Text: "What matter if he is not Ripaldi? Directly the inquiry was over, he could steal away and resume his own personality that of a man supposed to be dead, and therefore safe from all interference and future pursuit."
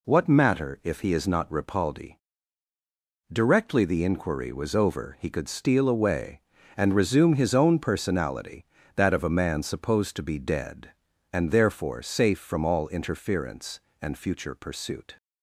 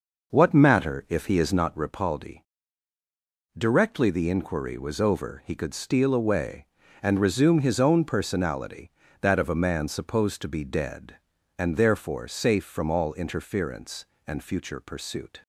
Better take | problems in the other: first | starts louder than the rest; noticeable; until 1.8 s; 5.5 dB

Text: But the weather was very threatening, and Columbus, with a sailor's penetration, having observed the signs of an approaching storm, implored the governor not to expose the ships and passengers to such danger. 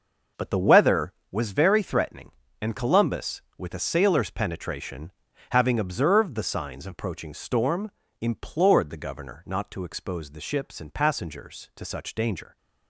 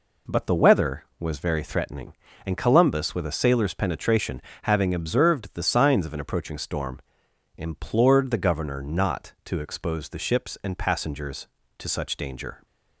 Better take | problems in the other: second | skips "an"; at 6.9 s

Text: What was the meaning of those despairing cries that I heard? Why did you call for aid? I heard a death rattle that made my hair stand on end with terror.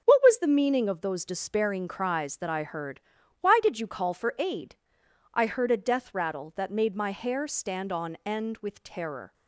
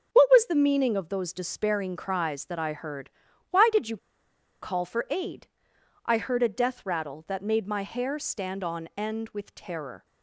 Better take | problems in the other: first | starts louder than the rest; until 1.1 s; 6 dB; also in the first // pauses between "you" and "call"; noticeable; at 3.9 s; 0.64 s long

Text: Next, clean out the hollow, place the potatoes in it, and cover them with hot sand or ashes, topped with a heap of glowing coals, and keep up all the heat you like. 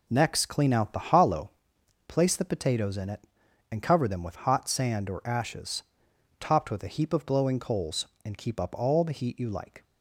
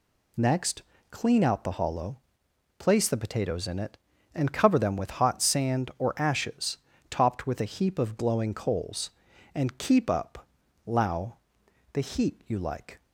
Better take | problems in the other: first | says "lao" for "all"; at 10.8 s

